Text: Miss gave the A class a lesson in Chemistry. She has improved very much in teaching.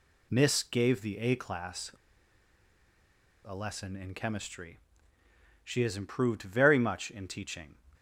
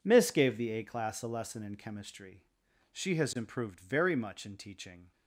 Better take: second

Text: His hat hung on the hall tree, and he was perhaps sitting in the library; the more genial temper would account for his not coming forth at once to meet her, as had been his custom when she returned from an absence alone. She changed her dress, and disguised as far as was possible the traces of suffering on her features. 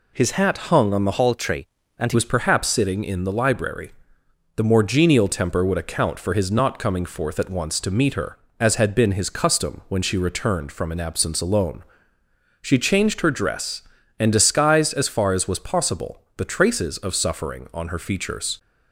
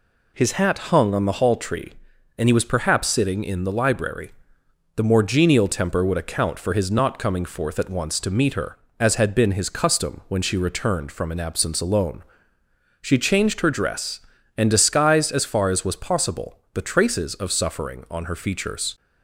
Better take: second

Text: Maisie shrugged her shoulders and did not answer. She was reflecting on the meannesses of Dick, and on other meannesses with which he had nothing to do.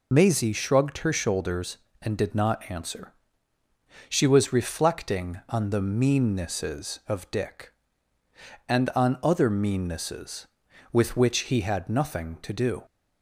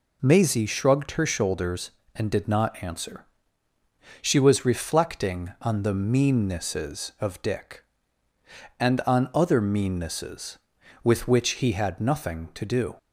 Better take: second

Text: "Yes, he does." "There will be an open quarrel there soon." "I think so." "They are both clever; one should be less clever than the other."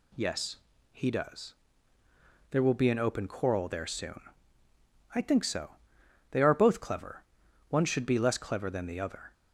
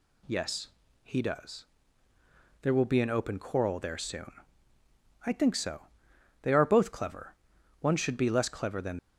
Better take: first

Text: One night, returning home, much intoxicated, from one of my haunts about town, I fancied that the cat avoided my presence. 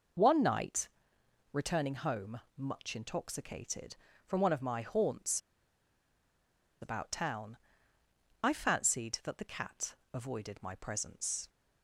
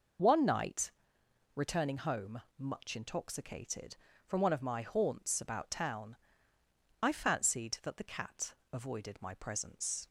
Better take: second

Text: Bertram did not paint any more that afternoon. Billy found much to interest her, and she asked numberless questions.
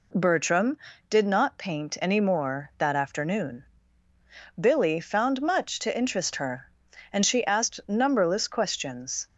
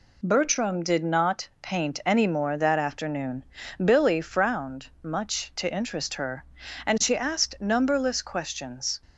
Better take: first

